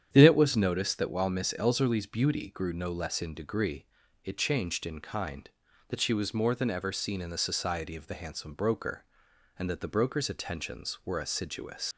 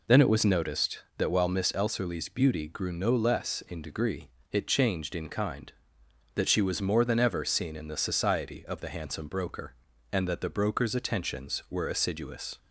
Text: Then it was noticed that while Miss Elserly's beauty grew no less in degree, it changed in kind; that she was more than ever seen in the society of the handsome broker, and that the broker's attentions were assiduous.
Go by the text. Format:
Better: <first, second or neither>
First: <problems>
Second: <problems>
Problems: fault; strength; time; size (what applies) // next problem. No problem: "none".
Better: second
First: starts louder than the rest; strong; until 1.1 s; 9 dB // leaves "assiduous" unfinished; at 11.9 s; 90 ms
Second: none